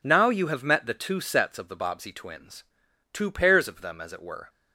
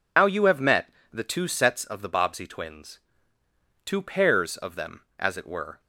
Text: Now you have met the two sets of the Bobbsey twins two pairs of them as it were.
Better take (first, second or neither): first